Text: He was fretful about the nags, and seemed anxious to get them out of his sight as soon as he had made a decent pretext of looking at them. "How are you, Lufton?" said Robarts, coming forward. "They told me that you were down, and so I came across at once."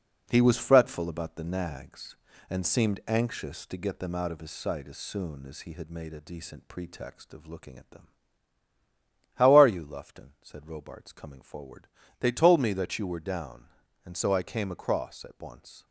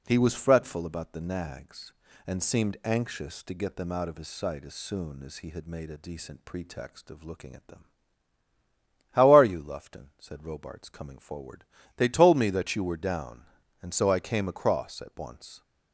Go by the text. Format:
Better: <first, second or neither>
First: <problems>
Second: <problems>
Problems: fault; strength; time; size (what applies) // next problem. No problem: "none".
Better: second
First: gets quieter; noticeable; throughout; 5.5 dB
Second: none